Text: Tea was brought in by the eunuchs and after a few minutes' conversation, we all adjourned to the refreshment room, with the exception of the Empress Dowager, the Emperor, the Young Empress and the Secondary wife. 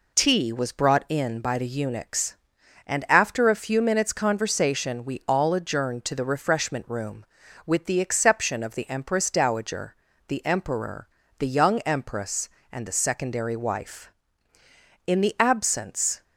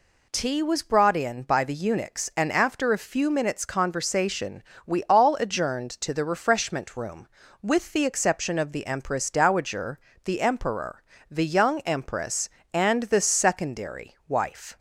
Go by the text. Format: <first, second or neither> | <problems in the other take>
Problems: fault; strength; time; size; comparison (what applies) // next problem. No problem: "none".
second | goes on to say "In the absence"; noticeable; from 15.0 s on; 1.1 s long